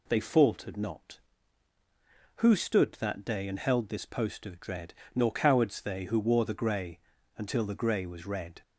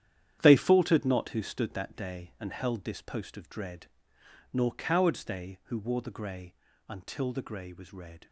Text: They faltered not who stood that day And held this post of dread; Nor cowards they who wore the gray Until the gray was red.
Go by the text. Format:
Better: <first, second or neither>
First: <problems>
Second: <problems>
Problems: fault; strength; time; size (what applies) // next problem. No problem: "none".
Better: first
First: pauses between "gray" and "Until"; slight; at 6.9 s; 0.36 s long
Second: gets quieter; strong; throughout; 10.5 dB // pauses between "gray" and "Until"; slight; at 6.5 s; 0.36 s long